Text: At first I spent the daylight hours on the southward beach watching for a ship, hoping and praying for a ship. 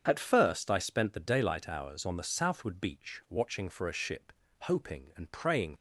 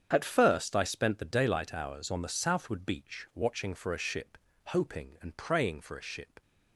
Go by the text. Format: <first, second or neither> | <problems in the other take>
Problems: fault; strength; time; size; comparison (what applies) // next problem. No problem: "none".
second | starts louder than the rest; strong; until 1.0 s; 7 dB; strong in the second // stops before "for a ship"; at 5.7 s